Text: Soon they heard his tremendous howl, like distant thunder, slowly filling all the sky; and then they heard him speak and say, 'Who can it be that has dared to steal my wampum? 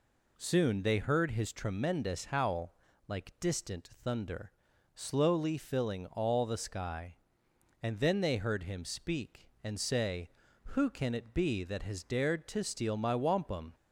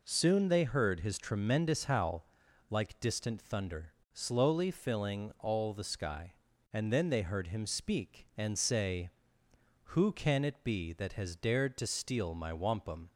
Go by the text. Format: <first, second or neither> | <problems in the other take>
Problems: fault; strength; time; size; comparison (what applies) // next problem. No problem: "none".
neither | none